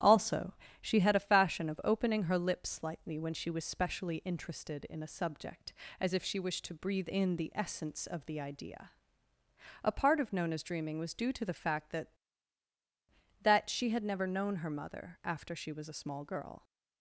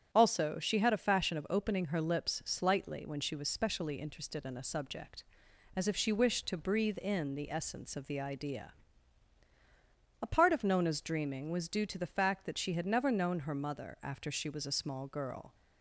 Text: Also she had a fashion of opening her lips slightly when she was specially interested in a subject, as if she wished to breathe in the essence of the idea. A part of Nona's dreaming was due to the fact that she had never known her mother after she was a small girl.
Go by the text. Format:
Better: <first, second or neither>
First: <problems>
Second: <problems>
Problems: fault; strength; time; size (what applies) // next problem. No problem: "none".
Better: second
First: starts louder than the rest; strong; until 1.3 s; 11.5 dB // pauses between "Also" and "she"; slight; at 0.5 s; 0.30 s long // says "that" twice; at 13.4 s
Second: starts louder than the rest; strong; until 1.1 s; 9 dB